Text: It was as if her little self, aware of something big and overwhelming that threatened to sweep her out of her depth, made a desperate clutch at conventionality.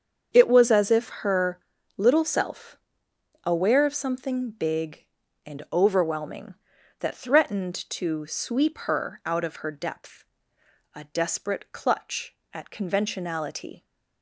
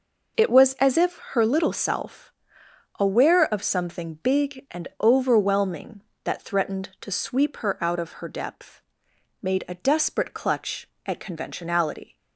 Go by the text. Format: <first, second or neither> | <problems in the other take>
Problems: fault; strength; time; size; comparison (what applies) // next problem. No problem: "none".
second | starts louder than the rest; strong; until 1.3 s; 7 dB // pauses between "her" and "little"; at 1.5 s; 0.40 s long // skips "made"; at 10.5 s